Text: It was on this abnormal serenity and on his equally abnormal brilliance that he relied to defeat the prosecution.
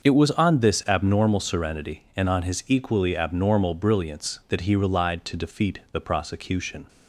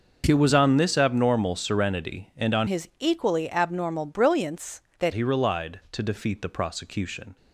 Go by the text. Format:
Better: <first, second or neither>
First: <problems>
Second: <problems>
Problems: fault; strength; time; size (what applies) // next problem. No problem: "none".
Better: first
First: starts louder than the rest; until 1.0 s; 6.5 dB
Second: starts louder than the rest; noticeable; until 1.2 s; 6 dB // changes voice from "his" to "that"; from 2.6 to 5.1 s; 2.5 s long